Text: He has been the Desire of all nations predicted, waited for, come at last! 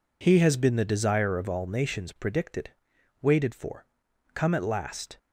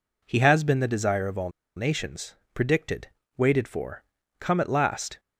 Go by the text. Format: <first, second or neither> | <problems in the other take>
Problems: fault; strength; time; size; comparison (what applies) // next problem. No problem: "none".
first | pauses between "all" and "nations"; slight; at 1.5 s; 0.25 s long // pauses between "nations" and "predicted"; slight; at 2.3 s; 0.18 s long